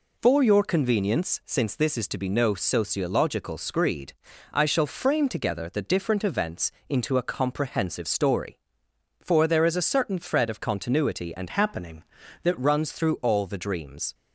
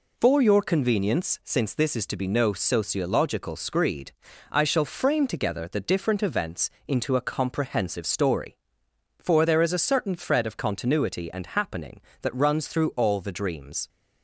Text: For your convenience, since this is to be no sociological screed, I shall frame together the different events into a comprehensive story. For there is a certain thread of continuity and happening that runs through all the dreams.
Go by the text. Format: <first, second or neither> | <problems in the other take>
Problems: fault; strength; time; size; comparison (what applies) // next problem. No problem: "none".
second | pauses between "events" and "into"; slight; at 6.7 s; 0.18 s long; slight in the second // changes voice from "happening" to "that"; from 11.4 to 12.5 s; 1.1 s long